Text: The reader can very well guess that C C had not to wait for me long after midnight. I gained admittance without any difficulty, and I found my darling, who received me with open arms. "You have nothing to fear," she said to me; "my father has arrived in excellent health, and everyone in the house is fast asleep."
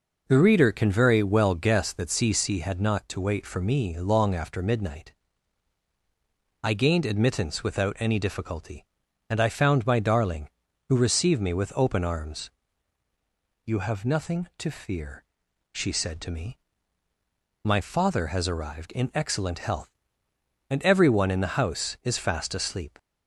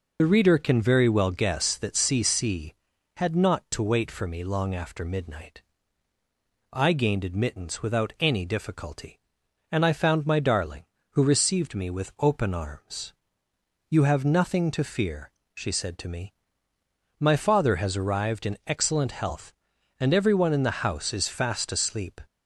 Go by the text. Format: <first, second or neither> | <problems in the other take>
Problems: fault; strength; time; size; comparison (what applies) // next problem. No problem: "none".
first | loses the start of "The"; at 0.1 s; 55 ms